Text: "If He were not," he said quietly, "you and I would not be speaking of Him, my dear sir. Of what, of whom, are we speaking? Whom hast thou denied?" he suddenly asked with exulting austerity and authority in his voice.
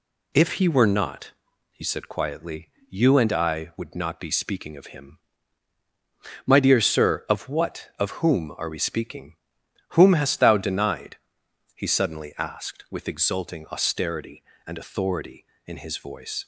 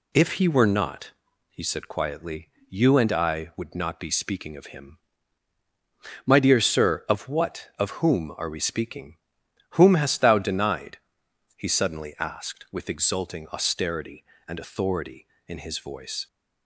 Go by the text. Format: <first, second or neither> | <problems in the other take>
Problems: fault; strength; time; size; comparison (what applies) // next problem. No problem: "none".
neither | none